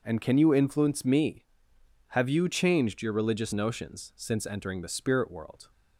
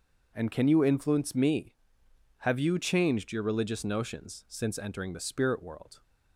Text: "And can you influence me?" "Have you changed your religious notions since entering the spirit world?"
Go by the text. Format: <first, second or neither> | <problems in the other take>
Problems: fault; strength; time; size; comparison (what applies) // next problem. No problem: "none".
neither | starts louder than the rest; the same in both